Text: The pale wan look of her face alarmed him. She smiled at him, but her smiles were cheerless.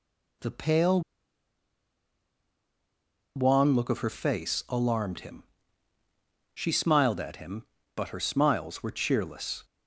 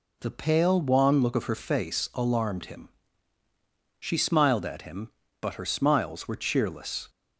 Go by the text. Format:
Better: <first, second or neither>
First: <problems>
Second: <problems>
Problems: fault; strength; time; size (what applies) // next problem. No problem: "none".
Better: second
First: pauses between "pale" and "wan"; strong; at 1.0 s; 2.3 s long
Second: none